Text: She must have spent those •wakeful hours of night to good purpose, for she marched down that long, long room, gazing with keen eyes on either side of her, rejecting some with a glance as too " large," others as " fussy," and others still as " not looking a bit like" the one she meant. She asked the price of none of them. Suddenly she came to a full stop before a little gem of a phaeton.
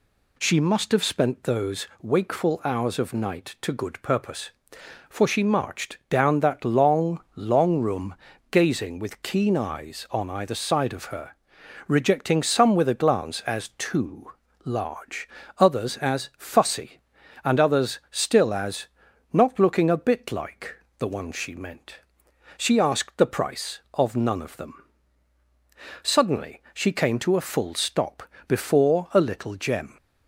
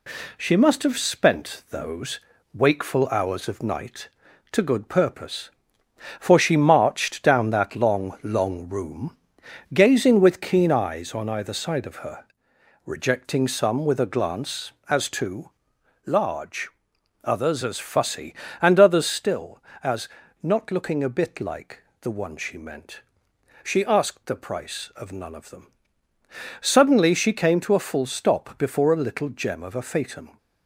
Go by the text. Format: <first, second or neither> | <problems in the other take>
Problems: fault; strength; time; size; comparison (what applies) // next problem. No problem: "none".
second | pauses between "like" and "the"; slight; at 20.7 s; 0.22 s long; slight in the second // pauses between "stop" and "before"; slight; at 28.2 s; 0.20 s long // stops before "of a phaeton"; at 29.9 s